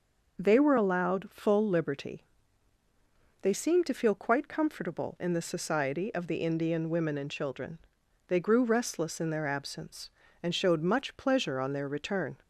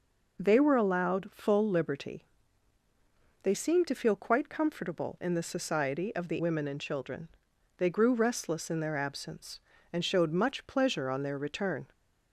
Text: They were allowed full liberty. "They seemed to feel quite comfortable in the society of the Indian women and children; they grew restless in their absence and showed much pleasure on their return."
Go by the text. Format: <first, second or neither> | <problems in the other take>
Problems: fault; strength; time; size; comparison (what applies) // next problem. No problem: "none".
first | skips "Indian"; at 6.4 s